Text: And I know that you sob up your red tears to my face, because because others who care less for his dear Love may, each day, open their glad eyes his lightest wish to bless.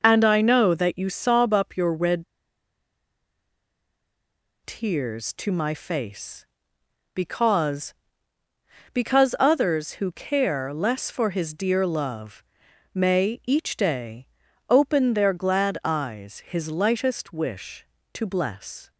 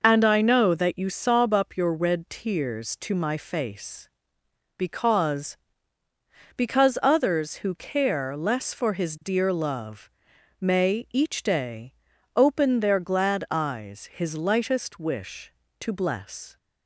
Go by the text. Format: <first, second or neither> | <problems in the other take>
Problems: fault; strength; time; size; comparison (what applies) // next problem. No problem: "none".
second | pauses between "red" and "tears"; strong; at 2.2 s; 2.3 s long // pauses between "Love" and "may"; noticeable; at 12.4 s; 0.50 s long; noticeable in the second